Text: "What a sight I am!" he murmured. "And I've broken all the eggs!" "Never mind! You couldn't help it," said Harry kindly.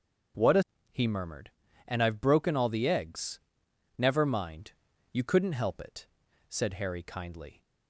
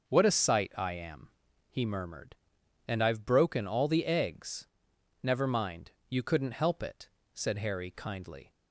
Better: second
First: starts louder than the rest; until 2.0 s; 7 dB // skips "sight I am"; at 0.7 s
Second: starts louder than the rest; noticeable; until 1.1 s; 6 dB

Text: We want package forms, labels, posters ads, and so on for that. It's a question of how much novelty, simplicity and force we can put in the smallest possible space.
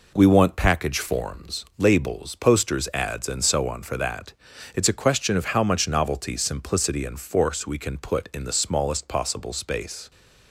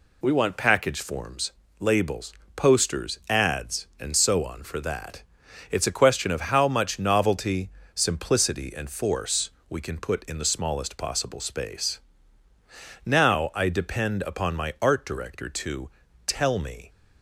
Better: first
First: none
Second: pauses between "force" and "we"; slight; at 9.4 s; 0.20 s long // goes on to say "Now I depend upon my art director to tell me"; strong; from 13.0 s on; 3.8 s long

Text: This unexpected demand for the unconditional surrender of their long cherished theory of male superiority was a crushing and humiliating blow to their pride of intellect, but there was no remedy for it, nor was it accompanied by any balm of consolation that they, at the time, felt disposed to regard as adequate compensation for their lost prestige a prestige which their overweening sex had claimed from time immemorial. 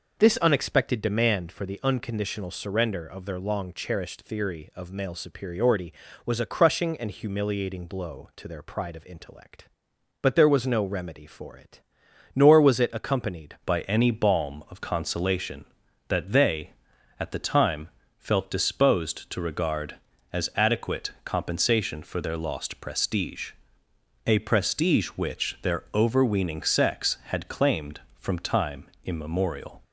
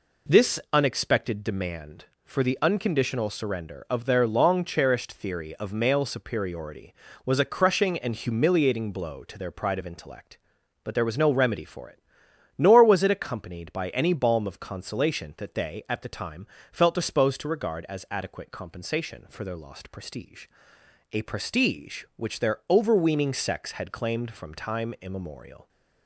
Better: second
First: changes voice at "by"; from 13.6 s on; 16.1 s long // pauses between "prestige" and "a"; noticeable; at 23.5 s; 0.74 s long // pauses between "time" and "immemorial"; slight; at 28.8 s; 0.18 s long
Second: pauses between "prestige" and "a"; noticeable; at 20.4 s; 0.66 s long

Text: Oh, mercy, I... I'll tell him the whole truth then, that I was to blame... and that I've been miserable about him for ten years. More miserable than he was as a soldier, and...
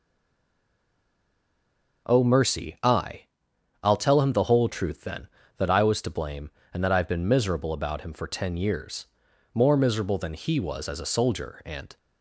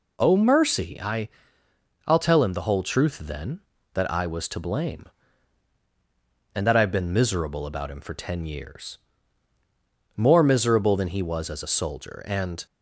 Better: second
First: stays silent before the first word; noticeable; until 2.0 s; 2.0 s long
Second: none

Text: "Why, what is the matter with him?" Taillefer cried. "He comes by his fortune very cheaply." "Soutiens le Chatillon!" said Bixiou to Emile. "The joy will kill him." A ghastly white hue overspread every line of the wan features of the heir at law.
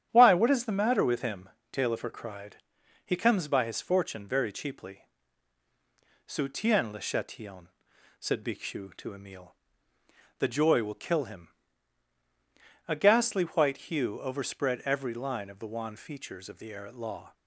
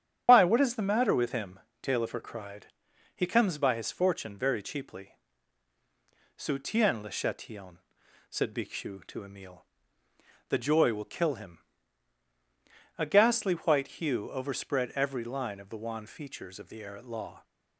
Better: first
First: starts louder than the rest; strong; until 1.1 s; 10 dB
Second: loses the start of "Why"; at 0.2 s; 75 ms // starts louder than the rest; strong; until 1.2 s; 9.5 dB

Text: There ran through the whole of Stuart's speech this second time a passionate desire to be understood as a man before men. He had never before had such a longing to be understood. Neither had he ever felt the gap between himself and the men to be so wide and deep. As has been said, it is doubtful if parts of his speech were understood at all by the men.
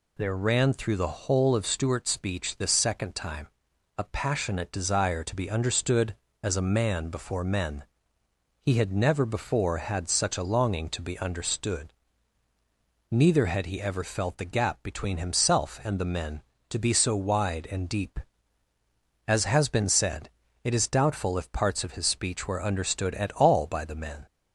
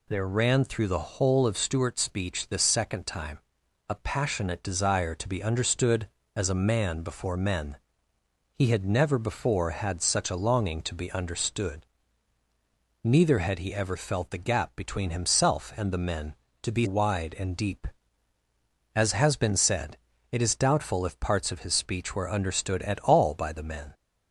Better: first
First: pauses between "time" and "a"; noticeable; at 3.4 s; 0.52 s long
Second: pauses between "time" and "a"; noticeable; at 3.3 s; 0.52 s long // skips "so"; at 16.8 s

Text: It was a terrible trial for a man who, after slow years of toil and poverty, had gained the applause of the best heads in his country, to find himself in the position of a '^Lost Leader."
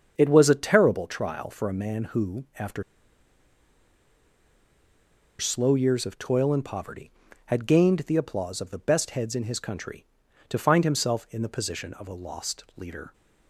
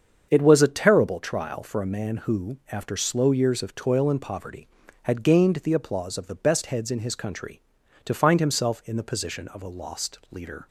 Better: second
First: starts louder than the rest; until 1.1 s; 7 dB // pauses between "after" and "slow"; strong; at 2.8 s; 2.5 s long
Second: starts louder than the rest; until 1.3 s; 7 dB

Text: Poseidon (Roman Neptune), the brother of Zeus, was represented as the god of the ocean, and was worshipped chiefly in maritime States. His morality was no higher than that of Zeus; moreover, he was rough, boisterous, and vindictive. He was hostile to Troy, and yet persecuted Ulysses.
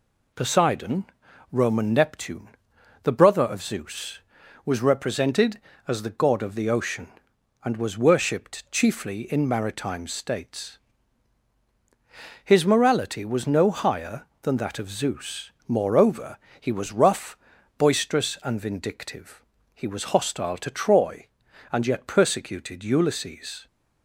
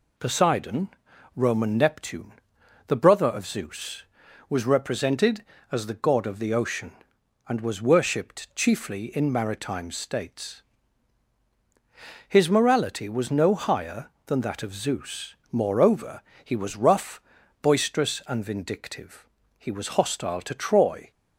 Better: first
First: none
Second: stops before "and yet persecuted Ulysses"; at 21.1 s

